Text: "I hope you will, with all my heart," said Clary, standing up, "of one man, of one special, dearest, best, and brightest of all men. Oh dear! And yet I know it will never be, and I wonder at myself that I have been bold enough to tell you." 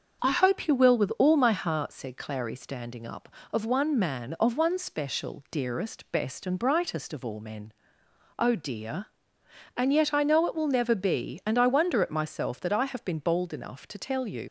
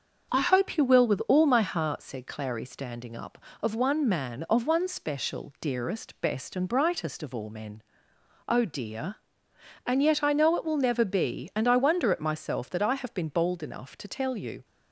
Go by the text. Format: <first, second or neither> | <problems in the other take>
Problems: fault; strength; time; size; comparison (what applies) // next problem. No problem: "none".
second | starts louder than the rest; until 1.2 s; 6.5 dB; also in the second // leaves "you" unfinished; at 14.4 s; 70 ms